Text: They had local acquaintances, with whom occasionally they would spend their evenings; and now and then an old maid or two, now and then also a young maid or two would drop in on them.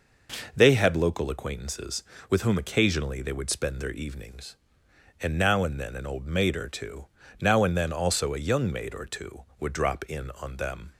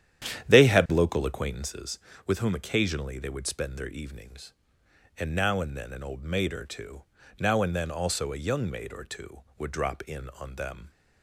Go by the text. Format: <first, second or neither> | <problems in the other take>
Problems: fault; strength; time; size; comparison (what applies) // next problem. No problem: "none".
first | starts louder than the rest; strong; until 1.7 s; 10 dB